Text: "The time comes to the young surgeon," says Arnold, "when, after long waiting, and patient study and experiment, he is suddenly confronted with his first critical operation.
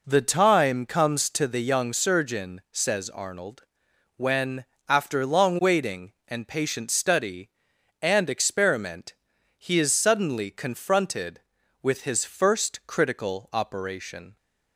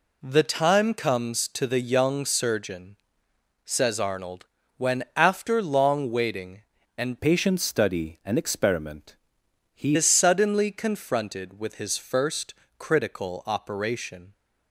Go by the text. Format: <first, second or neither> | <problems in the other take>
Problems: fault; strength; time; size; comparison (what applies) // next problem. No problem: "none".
first | changes voice from "patient" to "he"; from 7.1 to 9.9 s; 2.8 s long // pauses between "first" and "critical"; slight; at 12.5 s; 0.24 s long